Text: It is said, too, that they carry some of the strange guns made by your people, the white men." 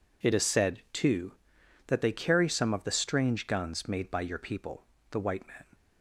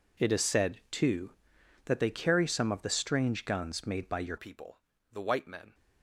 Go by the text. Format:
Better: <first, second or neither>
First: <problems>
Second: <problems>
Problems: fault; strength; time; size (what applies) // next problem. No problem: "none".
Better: first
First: none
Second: changes voice at "people"; from 4.3 s on; 1.4 s long